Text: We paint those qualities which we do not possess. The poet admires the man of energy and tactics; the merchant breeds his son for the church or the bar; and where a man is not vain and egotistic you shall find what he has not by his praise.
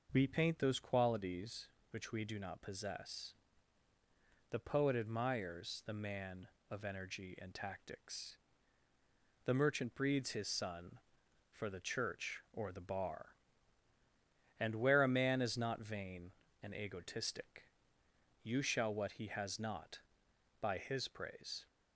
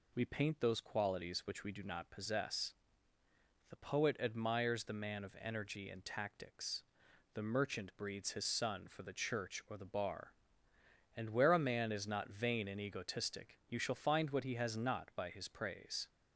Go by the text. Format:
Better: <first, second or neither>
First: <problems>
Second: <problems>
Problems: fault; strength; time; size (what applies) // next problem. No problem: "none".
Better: second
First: pauses between "egotistic" and "you"; noticeable; at 17.6 s; 0.76 s long // skips "find"; at 18.9 s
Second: none